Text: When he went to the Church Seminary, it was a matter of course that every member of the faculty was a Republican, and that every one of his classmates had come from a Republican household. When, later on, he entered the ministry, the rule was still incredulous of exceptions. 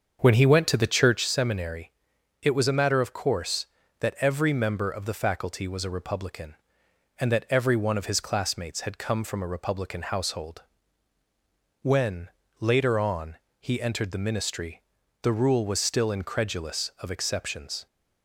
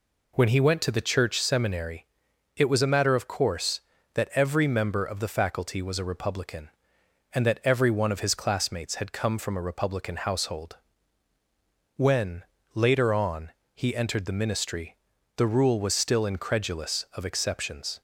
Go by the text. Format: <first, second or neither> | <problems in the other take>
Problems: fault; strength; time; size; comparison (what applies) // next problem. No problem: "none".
second | starts louder than the rest; until 1.2 s; 7 dB